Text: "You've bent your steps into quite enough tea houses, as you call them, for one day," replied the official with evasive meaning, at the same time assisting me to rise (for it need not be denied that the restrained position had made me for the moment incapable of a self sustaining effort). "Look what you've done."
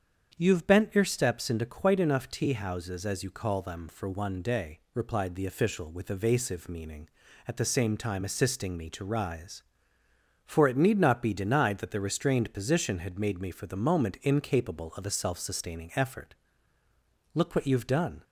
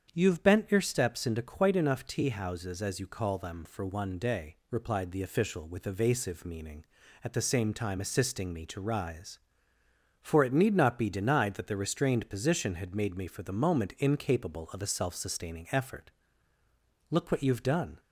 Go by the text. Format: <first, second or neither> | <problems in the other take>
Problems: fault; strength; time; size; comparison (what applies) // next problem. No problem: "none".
neither | starts louder than the rest; strong; the same in both